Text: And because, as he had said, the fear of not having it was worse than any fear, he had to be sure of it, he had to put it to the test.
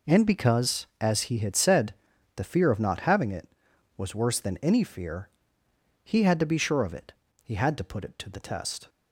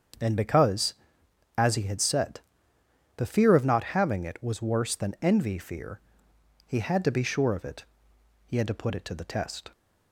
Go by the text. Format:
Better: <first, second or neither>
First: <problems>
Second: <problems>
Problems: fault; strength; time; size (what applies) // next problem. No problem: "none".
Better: first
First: none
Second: starts louder than the rest; strong; until 1.8 s; 7 dB // says "envy" for "any"; at 5.2 s